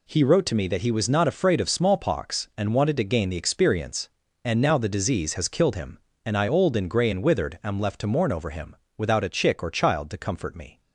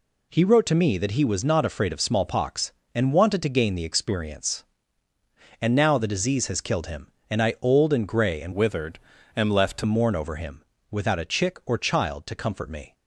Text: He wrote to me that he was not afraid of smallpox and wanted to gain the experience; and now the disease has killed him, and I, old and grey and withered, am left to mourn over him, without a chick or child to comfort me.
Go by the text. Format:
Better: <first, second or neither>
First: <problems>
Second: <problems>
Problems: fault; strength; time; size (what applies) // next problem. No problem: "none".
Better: first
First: none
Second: changes voice from "withered" to "to"; from 8.5 to 9.8 s; 1.3 s long